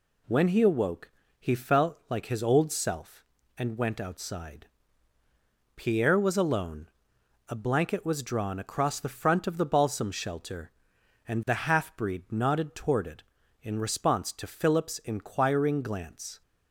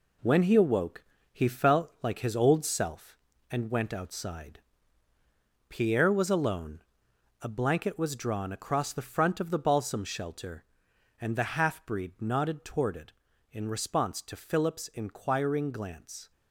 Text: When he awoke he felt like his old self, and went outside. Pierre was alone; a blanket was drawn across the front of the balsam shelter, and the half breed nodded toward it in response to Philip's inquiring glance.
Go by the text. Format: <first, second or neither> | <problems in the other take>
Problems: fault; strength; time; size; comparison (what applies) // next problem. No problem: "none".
first | gets quieter; throughout; 7 dB // pauses between "awoke" and "he"; slight; at 1.0 s; 0.28 s long; slight in the first